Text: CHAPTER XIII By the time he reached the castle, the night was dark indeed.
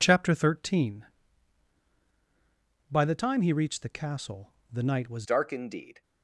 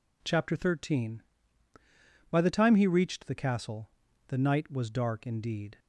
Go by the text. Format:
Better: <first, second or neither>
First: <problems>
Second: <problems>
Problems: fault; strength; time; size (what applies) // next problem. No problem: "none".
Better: second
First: changes voice at "dark"; from 5.2 s on; 0.8 s long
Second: none